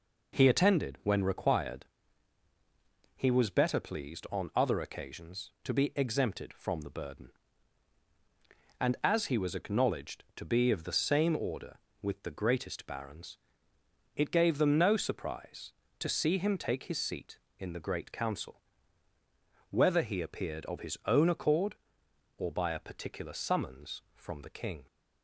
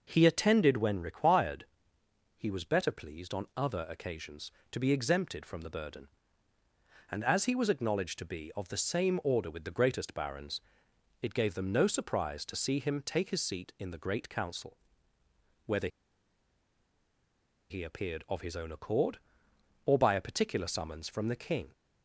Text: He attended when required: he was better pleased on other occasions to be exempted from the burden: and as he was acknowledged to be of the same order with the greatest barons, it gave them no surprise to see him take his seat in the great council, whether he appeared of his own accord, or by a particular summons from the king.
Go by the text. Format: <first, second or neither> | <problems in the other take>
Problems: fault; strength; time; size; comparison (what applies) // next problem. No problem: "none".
first | pauses between "whether" and "he"; strong; at 15.8 s; 1.8 s long